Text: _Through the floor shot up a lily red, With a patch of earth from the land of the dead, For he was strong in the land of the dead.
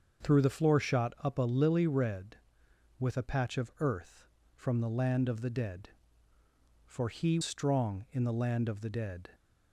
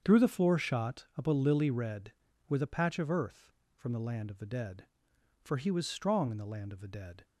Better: second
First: starts louder than the rest; until 1.3 s; 7 dB // skips "was"; at 7.4 s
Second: starts louder than the rest; strong; until 1.0 s; 7 dB

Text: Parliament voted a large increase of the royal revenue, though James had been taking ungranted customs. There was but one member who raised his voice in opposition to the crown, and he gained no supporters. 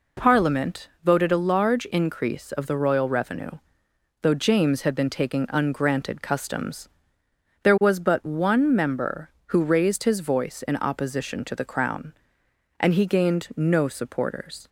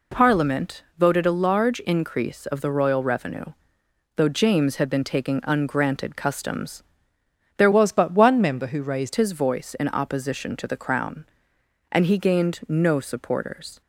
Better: first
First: pauses between "Parliament" and "voted"; slight; at 0.8 s; 0.16 s long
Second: pauses between "Parliament" and "voted"; slight; at 0.8 s; 0.16 s long // changes voice from "was" to "raised"; from 7.7 to 9.1 s; 1.4 s long

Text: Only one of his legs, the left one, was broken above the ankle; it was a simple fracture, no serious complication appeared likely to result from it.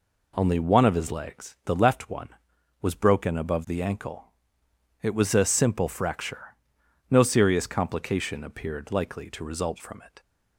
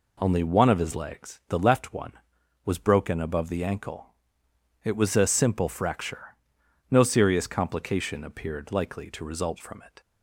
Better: neither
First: none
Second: none

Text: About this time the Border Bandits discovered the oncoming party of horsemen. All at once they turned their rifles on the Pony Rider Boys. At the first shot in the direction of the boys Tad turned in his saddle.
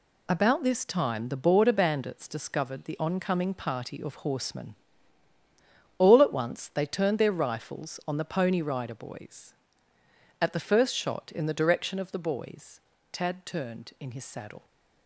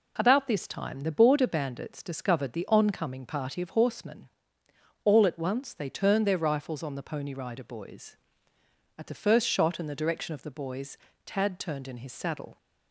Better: neither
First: pauses between "boys" and "Tad"; slight; at 12.8 s; 0.32 s long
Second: pauses between "boys" and "Tad"; slight; at 10.9 s; 0.30 s long

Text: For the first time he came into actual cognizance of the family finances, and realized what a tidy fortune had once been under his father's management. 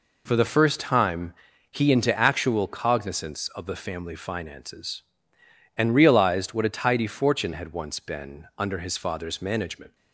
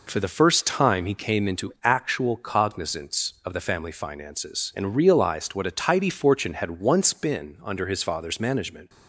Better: second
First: pauses between "time" and "he"; slight; at 1.3 s; 0.36 s long // skips "came"; at 1.9 s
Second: none

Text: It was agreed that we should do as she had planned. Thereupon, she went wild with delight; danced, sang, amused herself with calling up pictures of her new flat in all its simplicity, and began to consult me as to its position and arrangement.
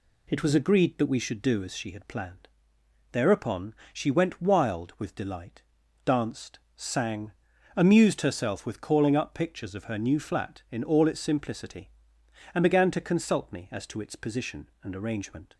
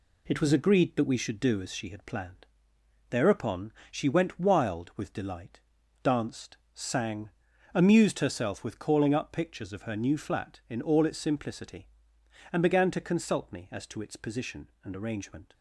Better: first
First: none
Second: gets quieter; noticeable; throughout; 5 dB

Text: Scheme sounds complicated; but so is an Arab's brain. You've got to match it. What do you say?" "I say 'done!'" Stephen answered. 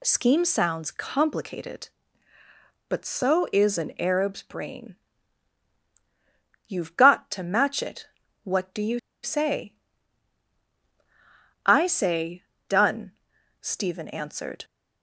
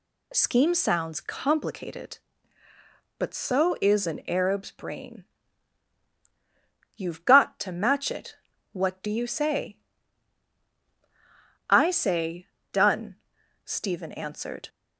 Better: second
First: pauses between "you" and "say"; slight; at 8.9 s; 0.24 s long // pauses between "say" and "done"; slight; at 12.4 s; 0.24 s long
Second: pauses between "say" and "done"; slight; at 12.4 s; 0.24 s long

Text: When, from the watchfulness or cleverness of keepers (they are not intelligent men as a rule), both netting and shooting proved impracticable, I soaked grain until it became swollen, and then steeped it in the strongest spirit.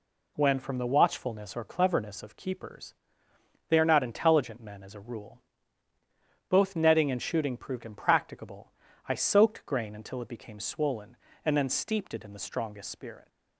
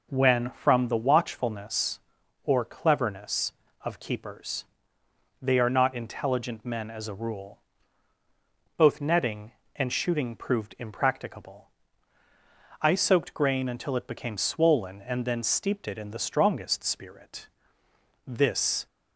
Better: first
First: none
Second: goes on to say "This"; from 18.2 s on; 0.60 s long

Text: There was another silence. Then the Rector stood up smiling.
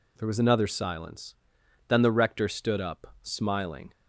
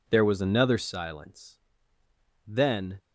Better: first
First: none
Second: stops before "the Rector stood up smiling"; at 2.9 s

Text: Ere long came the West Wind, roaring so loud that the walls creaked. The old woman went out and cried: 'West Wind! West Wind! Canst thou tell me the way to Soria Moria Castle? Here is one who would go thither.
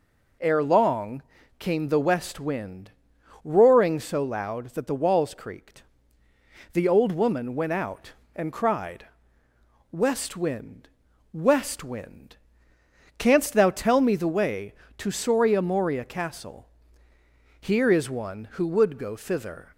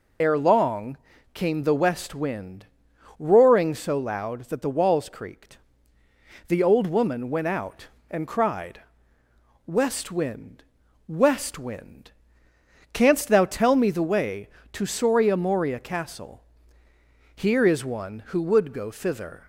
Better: first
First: pauses between "long" and "came"; slight; at 1.2 s; 0.36 s long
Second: loses the start of "Ere"; at 0.2 s; 50 ms // pauses between "long" and "came"; slight; at 0.9 s; 0.36 s long

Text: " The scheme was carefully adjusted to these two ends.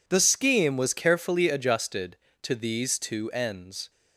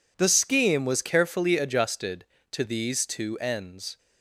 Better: neither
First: none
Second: none

